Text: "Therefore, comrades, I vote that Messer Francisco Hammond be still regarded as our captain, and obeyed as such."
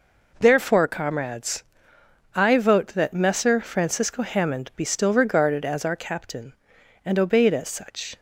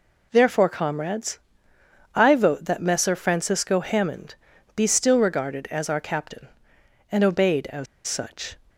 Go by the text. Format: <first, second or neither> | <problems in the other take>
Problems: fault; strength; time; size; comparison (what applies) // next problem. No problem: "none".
first | pauses between "Hammond" and "be"; at 4.3 s; 0.40 s long // pauses between "as" and "such"; slight; at 7.8 s; 0.21 s long